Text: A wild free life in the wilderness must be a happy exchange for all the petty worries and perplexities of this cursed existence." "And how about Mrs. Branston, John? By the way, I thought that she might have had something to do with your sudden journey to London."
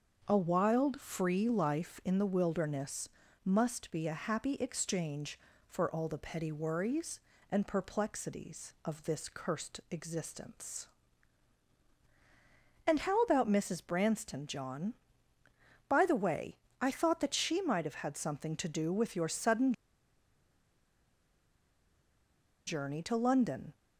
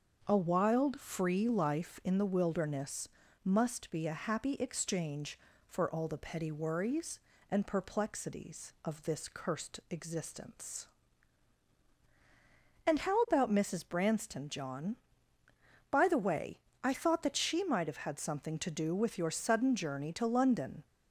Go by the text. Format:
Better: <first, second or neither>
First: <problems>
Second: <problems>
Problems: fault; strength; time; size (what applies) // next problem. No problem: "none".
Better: second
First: starts louder than the rest; until 1.2 s; 6.5 dB // pauses between "wilderness" and "must"; slight; at 3.0 s; 0.34 s long // pauses between "sudden" and "journey"; strong; at 19.7 s; 2.9 s long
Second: starts louder than the rest; until 1.2 s; 6.5 dB // pauses between "wilderness" and "must"; slight; at 3.0 s; 0.34 s long